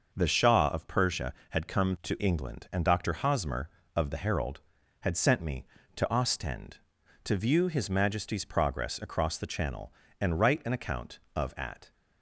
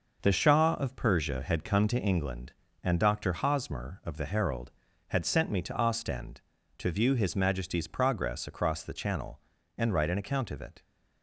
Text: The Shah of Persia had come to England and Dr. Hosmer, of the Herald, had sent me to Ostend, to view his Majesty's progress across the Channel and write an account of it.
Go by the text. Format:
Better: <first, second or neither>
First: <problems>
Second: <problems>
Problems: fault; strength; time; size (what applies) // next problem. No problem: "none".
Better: second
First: starts louder than the rest; noticeable; until 1.1 s; 6 dB // says "at" for "it"; at 11.5 s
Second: none